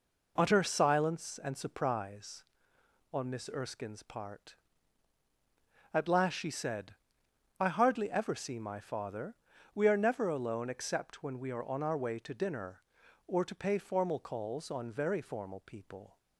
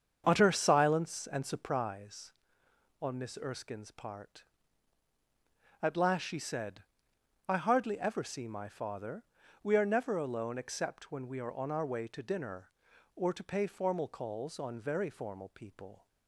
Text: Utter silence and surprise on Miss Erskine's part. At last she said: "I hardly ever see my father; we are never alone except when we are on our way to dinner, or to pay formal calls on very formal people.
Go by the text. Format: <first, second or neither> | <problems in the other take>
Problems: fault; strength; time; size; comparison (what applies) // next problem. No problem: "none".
first | starts louder than the rest; strong; until 1.7 s; 7.5 dB